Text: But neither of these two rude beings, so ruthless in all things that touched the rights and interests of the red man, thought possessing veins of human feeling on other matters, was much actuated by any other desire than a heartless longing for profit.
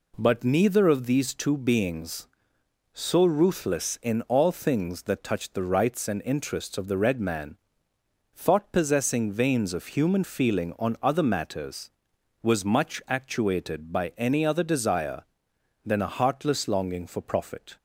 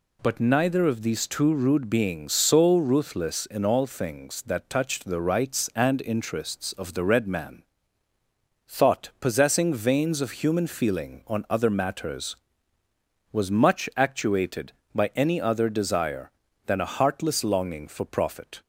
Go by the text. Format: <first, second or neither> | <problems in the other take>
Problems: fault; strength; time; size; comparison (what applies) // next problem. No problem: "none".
second | skips "rude"; at 1.5 s